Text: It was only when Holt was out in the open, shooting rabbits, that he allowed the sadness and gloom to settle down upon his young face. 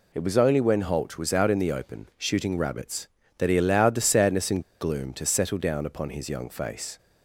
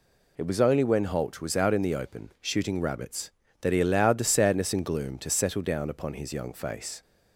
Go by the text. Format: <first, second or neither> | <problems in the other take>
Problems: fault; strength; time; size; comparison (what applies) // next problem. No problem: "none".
second | pauses between "and" and "gloom"; slight; at 4.6 s; 0.18 s long